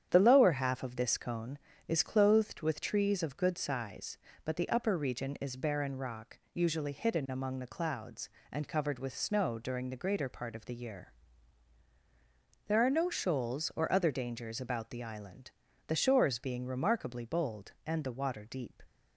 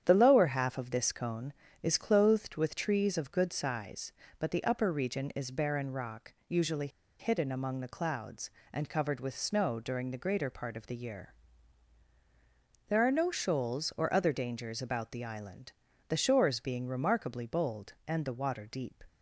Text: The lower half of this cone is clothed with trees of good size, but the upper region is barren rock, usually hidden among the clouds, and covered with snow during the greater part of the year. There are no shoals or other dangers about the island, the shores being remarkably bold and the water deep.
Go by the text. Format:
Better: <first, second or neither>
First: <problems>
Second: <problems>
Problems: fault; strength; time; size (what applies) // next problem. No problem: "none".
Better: first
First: starts louder than the rest; strong; until 1.1 s; 9 dB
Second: starts louder than the rest; strong; until 1.0 s; 9 dB // pauses between "usually" and "hidden"; slight; at 6.8 s; 0.31 s long